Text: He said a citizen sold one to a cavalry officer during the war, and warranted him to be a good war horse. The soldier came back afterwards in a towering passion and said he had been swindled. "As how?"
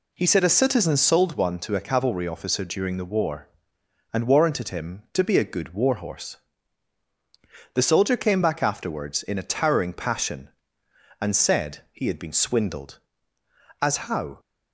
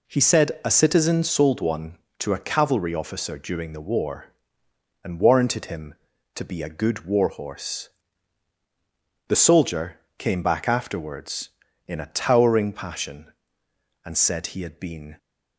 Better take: first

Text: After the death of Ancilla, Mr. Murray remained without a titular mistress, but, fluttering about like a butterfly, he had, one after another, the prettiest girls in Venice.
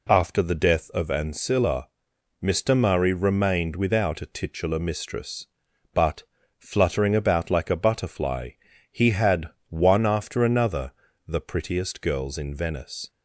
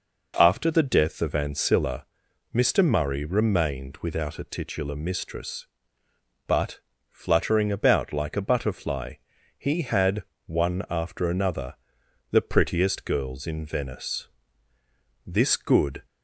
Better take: first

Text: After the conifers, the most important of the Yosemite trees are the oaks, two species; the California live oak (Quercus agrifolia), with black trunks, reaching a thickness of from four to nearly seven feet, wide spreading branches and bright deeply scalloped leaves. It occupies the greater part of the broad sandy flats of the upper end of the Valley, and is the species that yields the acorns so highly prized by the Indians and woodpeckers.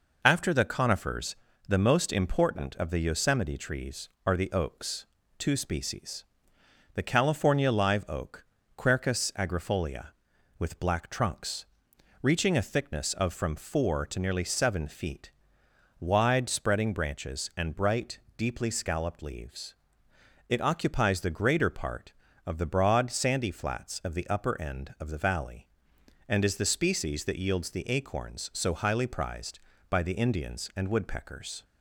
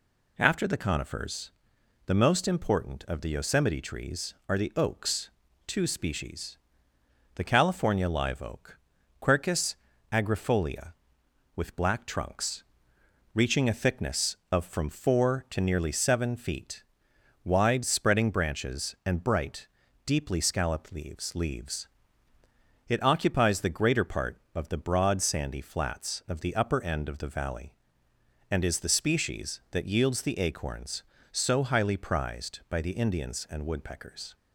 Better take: first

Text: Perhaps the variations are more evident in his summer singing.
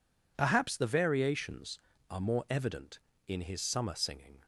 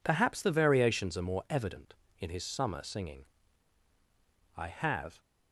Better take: first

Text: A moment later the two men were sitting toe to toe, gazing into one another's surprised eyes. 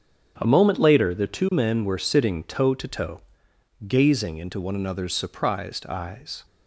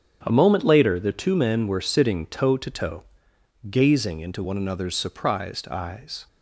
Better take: neither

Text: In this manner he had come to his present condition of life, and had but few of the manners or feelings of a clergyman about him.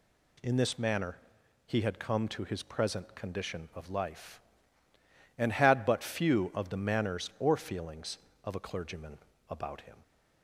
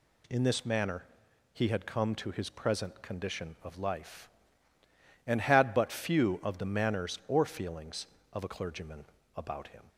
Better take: neither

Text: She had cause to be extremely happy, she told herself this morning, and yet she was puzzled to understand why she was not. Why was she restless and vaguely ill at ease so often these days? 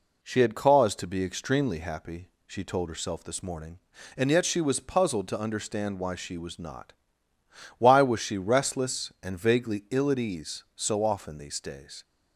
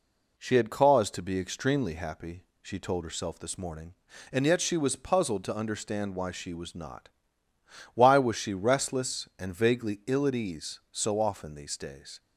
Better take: neither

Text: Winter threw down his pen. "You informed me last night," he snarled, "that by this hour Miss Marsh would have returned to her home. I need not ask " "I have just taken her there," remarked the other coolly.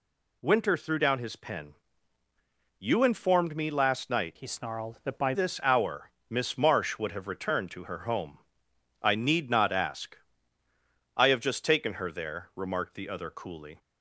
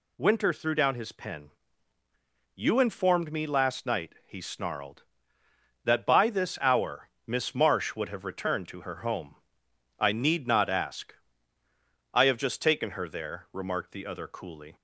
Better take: second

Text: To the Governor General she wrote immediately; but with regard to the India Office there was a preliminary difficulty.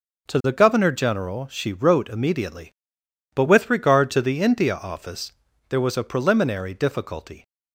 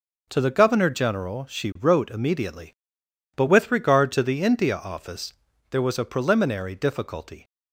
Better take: neither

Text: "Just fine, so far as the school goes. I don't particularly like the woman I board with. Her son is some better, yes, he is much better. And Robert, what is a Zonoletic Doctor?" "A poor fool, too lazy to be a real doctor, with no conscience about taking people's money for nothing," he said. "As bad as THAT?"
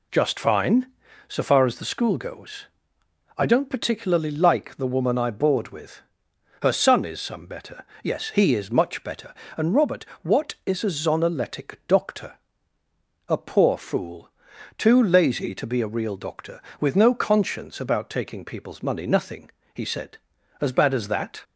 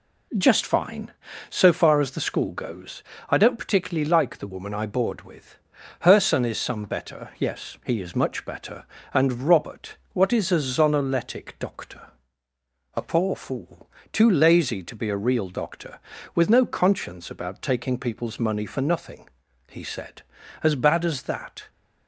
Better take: second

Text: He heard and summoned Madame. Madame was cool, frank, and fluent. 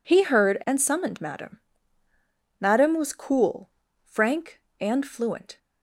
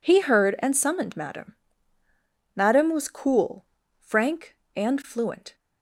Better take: neither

